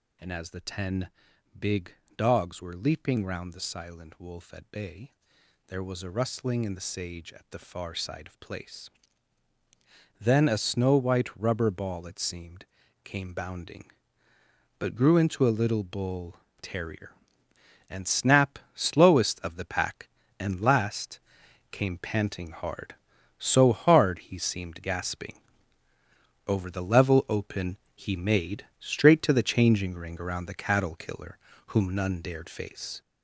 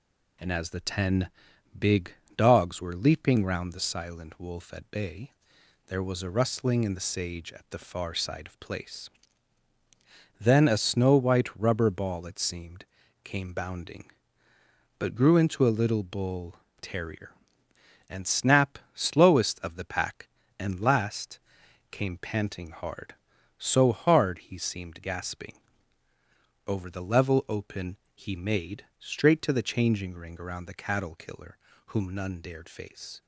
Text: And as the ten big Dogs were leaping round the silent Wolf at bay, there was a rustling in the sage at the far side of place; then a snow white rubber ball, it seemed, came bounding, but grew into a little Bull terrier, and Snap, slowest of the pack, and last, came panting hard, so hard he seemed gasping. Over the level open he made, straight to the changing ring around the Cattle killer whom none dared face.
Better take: second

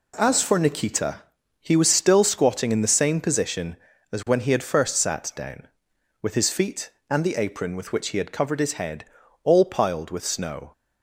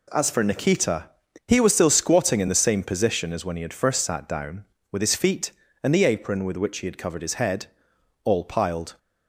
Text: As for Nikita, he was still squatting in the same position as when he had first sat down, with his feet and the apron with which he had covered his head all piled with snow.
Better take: first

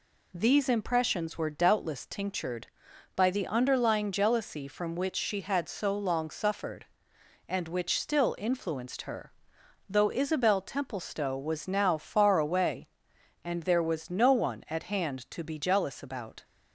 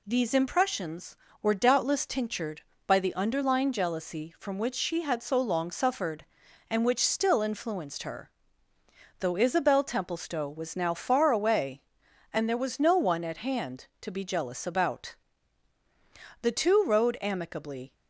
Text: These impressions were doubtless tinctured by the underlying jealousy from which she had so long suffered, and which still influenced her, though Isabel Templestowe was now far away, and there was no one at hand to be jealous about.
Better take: first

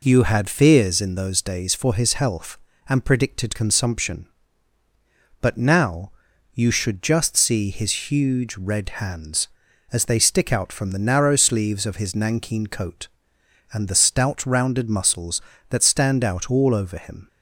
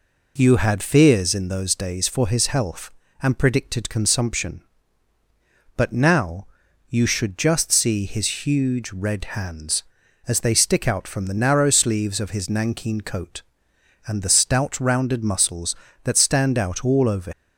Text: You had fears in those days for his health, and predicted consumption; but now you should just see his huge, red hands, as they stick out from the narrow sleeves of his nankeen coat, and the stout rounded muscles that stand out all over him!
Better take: first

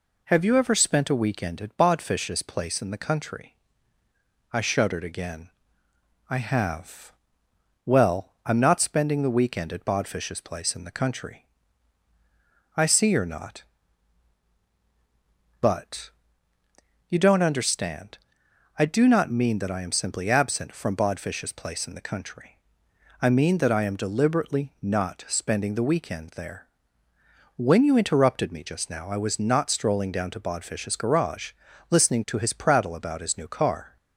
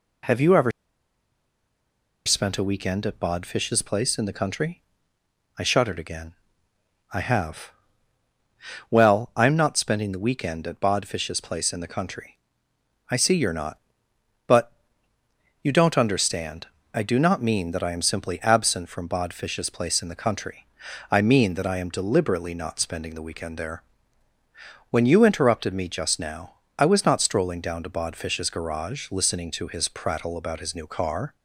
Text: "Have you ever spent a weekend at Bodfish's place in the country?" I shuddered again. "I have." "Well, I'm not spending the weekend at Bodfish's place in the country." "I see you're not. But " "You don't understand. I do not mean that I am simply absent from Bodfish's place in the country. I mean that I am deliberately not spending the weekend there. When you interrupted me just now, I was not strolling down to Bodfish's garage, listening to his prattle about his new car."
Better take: first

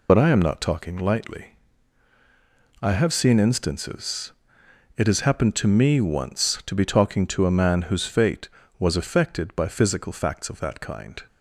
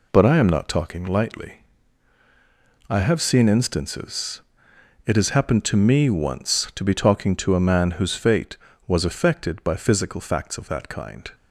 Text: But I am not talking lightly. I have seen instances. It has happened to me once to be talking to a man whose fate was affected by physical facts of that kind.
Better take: second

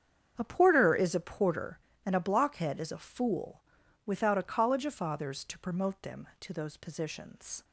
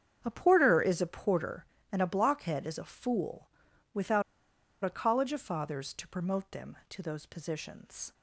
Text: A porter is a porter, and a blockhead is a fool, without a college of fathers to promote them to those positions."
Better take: first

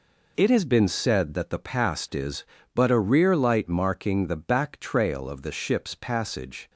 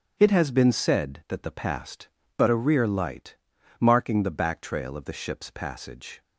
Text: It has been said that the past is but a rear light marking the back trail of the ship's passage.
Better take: first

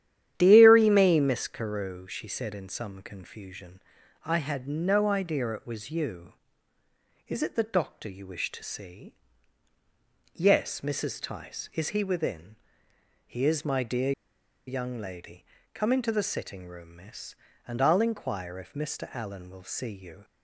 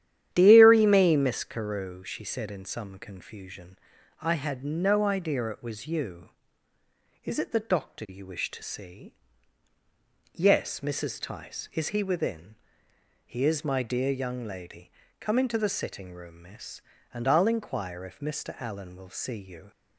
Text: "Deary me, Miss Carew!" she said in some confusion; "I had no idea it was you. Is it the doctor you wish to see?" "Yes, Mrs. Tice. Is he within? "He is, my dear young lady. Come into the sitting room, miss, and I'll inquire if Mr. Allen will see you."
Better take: second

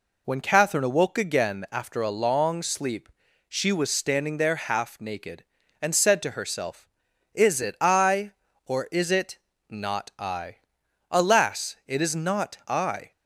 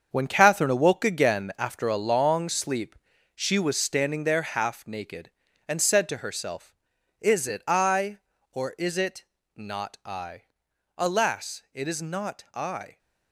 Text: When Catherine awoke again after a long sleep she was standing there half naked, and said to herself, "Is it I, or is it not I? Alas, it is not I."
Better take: first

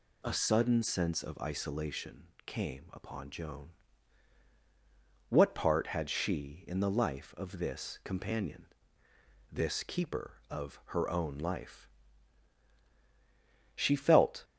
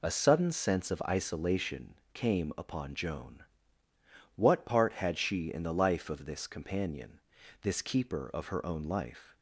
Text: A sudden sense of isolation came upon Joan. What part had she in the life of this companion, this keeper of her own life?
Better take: second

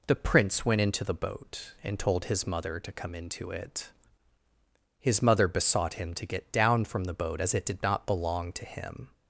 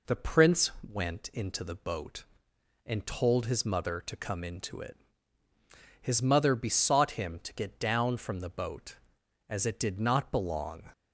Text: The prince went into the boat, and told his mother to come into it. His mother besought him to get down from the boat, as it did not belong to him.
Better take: first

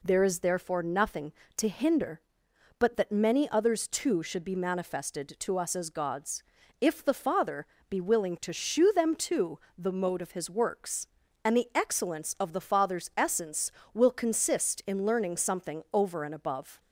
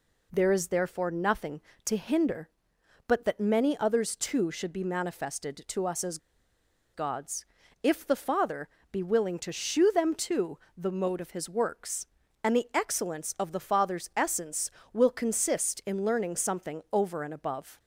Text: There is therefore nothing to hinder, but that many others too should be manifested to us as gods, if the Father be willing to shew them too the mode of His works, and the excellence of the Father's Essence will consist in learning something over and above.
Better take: first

